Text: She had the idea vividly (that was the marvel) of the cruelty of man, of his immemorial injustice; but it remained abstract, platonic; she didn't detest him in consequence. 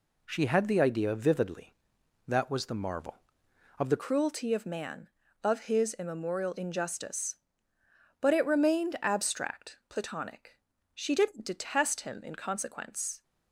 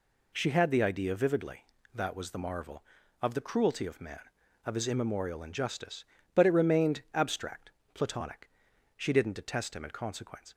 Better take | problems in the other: second | changes voice at "cruelty"; from 3.9 s on; 9.3 s long

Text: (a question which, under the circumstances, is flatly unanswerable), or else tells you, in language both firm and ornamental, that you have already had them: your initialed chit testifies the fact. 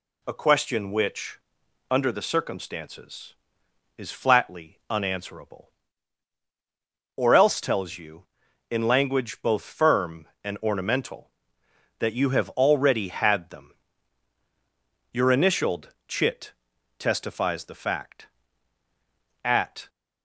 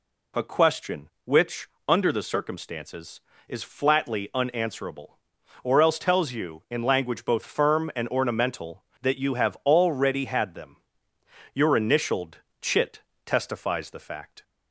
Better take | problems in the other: second | pauses between "initialed" and "chit"; slight; at 15.8 s; 0.18 s long; slight in the second // pauses between "chit" and "testifies"; noticeable; at 16.5 s; 0.66 s long; slight in the second // goes on to say "At"; slight; from 19.4 s on; 0.46 s long

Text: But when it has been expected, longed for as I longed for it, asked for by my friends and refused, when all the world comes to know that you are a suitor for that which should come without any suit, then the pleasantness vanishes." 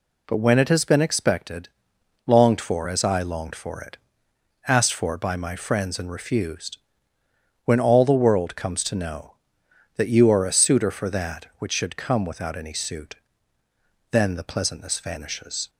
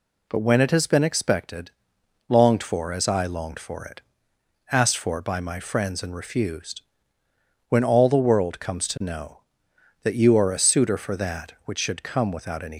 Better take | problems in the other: first | stops before "suit then the pleasantness vanishes"; at 12.7 s

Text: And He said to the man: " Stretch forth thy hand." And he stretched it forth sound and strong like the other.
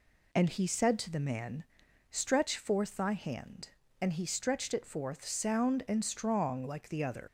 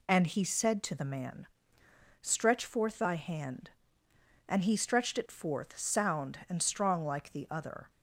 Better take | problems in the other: second | leaves "other" unfinished; at 7.2 s; 100 ms

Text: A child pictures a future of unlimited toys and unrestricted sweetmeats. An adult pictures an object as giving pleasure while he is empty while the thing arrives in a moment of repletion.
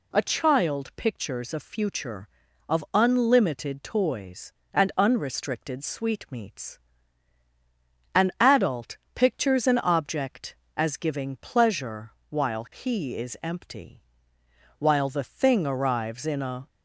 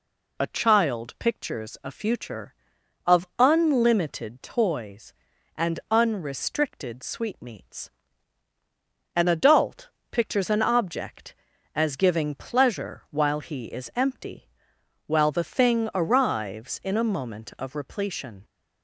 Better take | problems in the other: second | pauses between "adult" and "pictures"; slight; at 8.9 s; 0.18 s long; slight in the second // pauses between "pleasure" and "while"; slight; at 12.1 s; 0.18 s long // pauses between "empty" and "while"; noticeable; at 14.0 s; 0.78 s long; noticeable in the second // stops before "moment of repletion"; at 16.6 s

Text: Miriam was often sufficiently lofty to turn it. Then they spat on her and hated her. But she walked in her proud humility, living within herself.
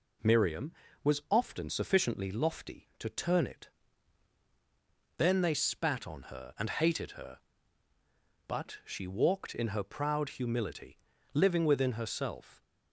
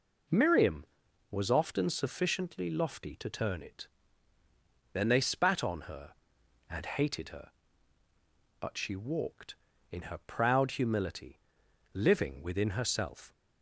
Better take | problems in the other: neither | none

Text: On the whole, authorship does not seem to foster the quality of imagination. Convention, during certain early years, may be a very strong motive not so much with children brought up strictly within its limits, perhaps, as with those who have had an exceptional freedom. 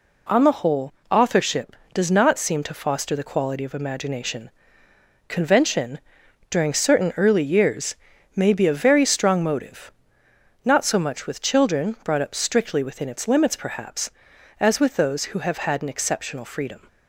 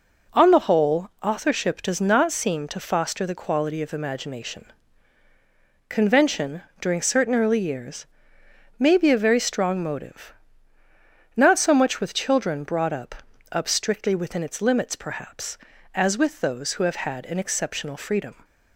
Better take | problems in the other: first | pauses between "motive" and "not"; at 10.3 s; 1.0 s long; noticeable in the first // says "up" twice; at 13.5 s

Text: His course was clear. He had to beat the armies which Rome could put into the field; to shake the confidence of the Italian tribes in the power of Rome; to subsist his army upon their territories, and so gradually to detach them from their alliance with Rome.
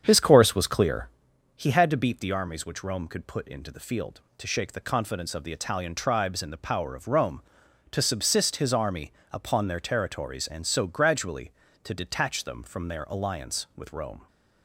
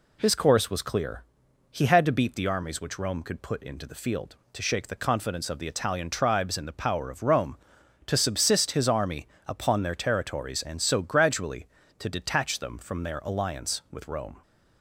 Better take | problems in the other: second | starts louder than the rest; strong; until 1.4 s; 8 dB // pauses between "army" and "upon"; slight; at 9.1 s; 0.20 s long; slight in the second

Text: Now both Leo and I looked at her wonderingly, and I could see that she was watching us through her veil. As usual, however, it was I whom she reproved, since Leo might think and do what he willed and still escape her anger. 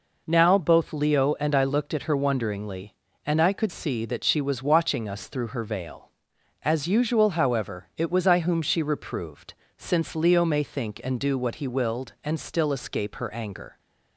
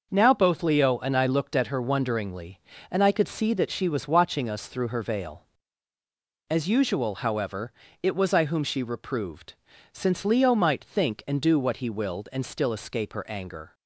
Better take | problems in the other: second | says "may" for "might"; at 10.4 s

